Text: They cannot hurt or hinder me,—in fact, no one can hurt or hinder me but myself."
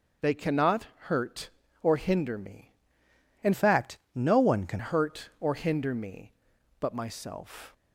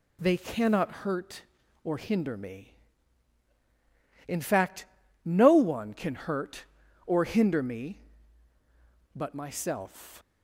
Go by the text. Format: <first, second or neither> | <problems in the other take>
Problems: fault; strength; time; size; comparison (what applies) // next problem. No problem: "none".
second | starts louder than the rest; until 1.3 s; 6.5 dB // pauses between "cannot" and "hurt"; slight; at 0.8 s; 0.16 s long // changes voice from "fact" to "can"; from 3.5 to 4.7 s; 1.2 s long